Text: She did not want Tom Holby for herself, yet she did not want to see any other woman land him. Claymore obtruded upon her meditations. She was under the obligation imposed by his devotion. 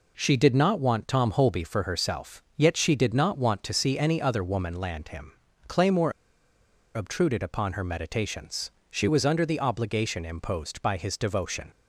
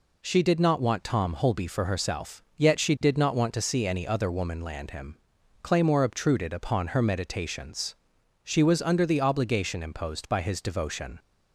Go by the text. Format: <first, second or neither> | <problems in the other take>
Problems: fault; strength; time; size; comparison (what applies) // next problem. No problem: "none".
second | pauses between "Claymore" and "obtruded"; noticeable; at 6.1 s; 0.82 s long